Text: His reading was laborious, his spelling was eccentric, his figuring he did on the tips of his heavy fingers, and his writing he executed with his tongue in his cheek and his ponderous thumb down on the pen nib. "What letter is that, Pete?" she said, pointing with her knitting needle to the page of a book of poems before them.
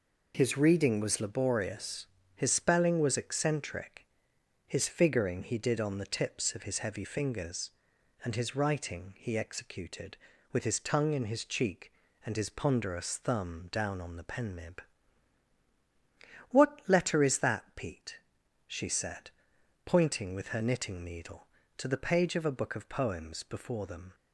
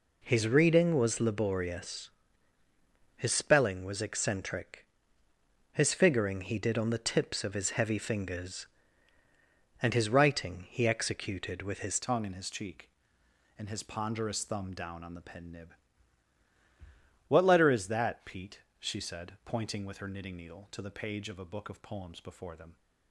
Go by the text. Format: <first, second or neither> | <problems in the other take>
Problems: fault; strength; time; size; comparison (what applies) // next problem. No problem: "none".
first | changes voice at "tongue"; from 12.0 s on; 10.7 s long